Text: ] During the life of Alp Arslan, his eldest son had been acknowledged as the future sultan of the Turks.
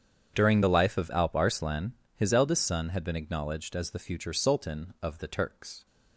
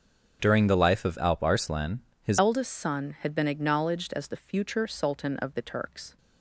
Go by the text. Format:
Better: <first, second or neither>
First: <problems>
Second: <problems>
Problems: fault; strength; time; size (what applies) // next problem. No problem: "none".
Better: first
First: starts louder than the rest; strong; until 1.3 s; 8 dB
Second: starts louder than the rest; until 1.4 s; 7 dB // changes voice at "eldest"; from 2.3 s on; 3.8 s long